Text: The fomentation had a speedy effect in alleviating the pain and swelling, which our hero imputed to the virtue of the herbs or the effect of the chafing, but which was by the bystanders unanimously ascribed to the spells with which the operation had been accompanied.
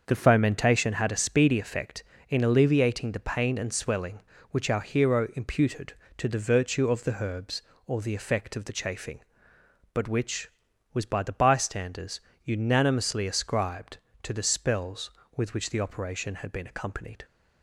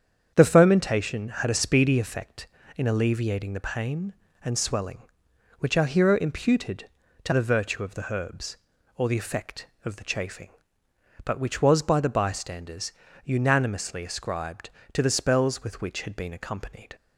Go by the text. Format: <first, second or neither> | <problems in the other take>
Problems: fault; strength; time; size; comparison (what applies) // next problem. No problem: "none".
first | starts louder than the rest; strong; until 1.3 s; 8 dB; also in the first // pauses between "bystanders" and "unanimously"; slight; at 12.9 s; 0.34 s long; slight in the first // skips "the operation"; at 16.0 s